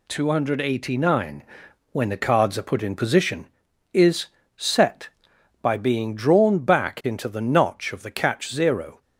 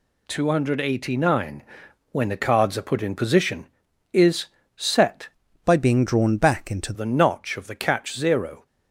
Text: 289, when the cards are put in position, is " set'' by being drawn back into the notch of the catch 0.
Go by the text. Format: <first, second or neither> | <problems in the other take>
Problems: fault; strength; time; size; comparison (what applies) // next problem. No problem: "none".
first | changes voice from "by" to "into"; from 5.6 to 6.9 s; 1.3 s long